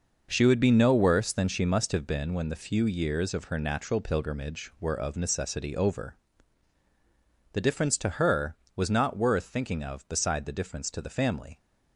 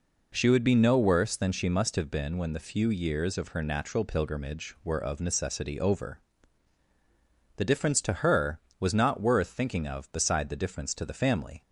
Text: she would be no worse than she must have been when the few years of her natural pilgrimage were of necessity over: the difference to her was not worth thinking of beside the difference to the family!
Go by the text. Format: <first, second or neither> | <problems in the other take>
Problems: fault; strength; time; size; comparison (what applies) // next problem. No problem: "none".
second | gets quieter; strong; throughout; 9 dB